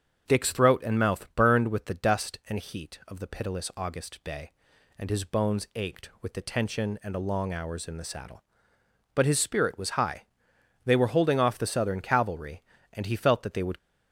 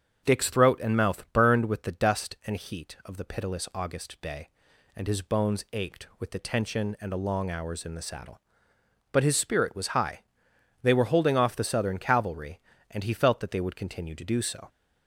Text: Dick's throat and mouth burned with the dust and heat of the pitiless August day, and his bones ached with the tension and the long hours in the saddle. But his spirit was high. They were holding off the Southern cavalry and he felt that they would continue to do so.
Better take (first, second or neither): second